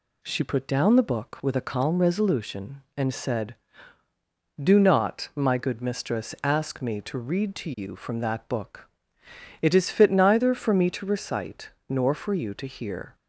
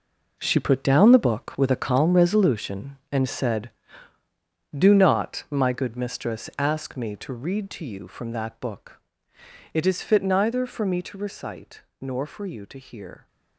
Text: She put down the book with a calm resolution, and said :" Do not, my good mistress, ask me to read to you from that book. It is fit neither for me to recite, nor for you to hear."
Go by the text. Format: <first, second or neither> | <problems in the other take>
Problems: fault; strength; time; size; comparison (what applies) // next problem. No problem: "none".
first | gets quieter; throughout; 7 dB